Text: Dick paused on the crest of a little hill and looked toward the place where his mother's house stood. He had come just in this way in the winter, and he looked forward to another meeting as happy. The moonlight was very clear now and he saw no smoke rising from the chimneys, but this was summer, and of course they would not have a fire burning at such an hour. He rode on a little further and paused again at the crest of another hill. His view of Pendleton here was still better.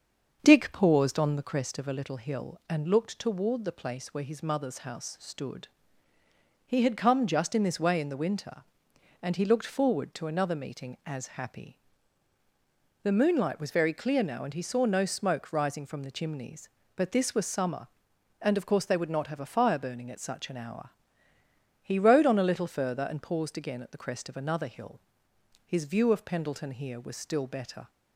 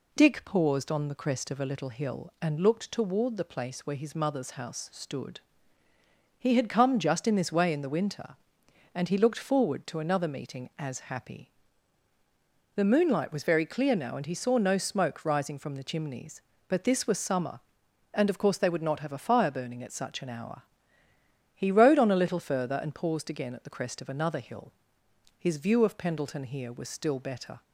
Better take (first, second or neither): second